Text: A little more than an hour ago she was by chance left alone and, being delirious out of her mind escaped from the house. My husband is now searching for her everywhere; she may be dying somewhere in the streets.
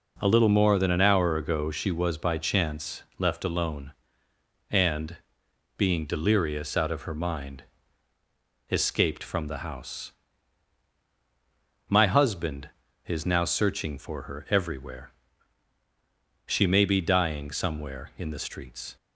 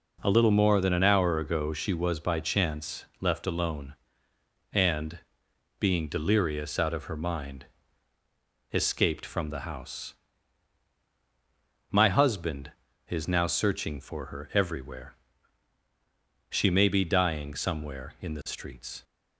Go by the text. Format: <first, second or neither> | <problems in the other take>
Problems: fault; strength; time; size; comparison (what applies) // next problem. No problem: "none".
neither | pauses between "chance" and "left"; slight; the same in both // pauses between "mind" and "escaped"; the same in both